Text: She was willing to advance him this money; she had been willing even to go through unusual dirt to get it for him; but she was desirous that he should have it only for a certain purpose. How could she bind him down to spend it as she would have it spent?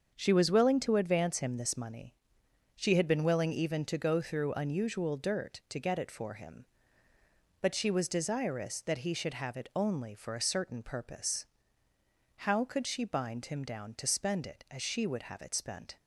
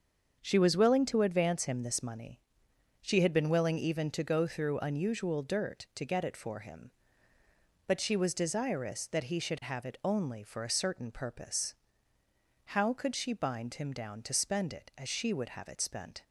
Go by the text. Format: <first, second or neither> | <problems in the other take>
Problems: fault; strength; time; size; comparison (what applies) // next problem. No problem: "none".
neither | starts louder than the rest; the same in both